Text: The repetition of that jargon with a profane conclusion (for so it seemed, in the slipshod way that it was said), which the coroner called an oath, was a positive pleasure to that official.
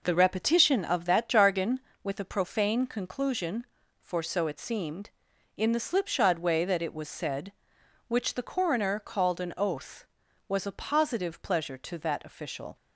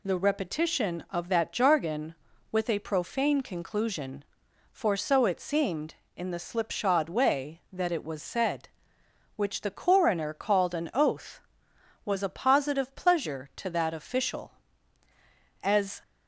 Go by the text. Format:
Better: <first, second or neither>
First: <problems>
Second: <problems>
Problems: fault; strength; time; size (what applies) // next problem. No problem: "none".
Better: first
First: none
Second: goes on to say "As"; slight; from 15.6 s on; 0.40 s long